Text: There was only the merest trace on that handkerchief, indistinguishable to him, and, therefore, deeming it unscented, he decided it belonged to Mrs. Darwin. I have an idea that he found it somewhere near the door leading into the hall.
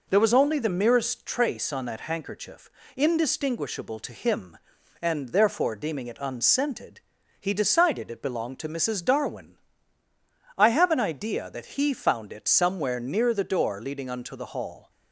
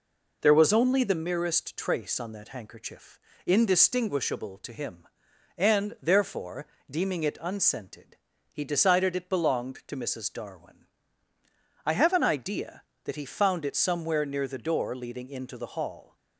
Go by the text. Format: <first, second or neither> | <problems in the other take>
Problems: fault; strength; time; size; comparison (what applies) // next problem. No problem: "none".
second | says "unto" for "into"; at 14.0 s